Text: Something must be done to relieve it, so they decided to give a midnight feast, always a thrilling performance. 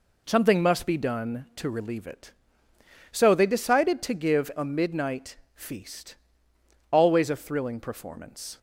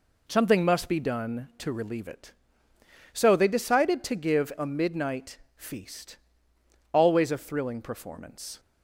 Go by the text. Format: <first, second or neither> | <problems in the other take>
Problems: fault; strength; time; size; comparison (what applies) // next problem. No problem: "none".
neither | pauses between "midnight" and "feast"; slight; the same in both